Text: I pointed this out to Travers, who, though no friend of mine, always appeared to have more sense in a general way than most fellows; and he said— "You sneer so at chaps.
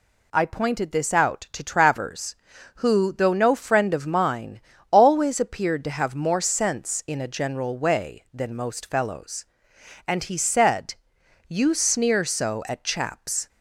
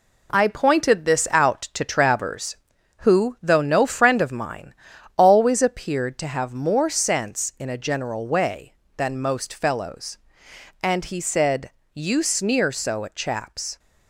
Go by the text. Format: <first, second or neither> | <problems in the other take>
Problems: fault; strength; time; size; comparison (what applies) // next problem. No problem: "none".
first | gets quieter; throughout; 6.5 dB